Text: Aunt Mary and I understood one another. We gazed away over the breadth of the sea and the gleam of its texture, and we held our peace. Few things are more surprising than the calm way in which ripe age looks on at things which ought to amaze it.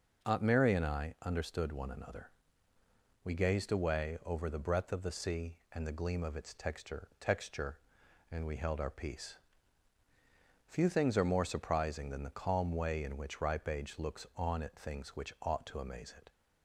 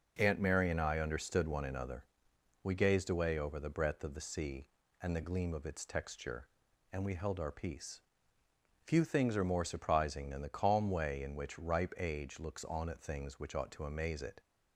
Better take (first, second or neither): second